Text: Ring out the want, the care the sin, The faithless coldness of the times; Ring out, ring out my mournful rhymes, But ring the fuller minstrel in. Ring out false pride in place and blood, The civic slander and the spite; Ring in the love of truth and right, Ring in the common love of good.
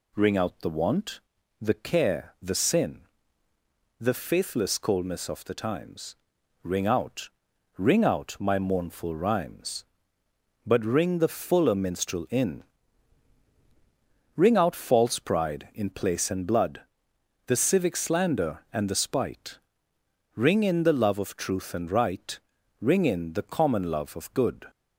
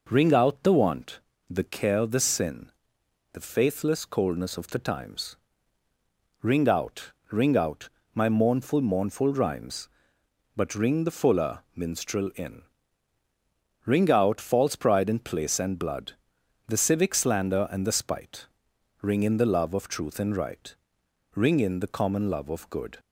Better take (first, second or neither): first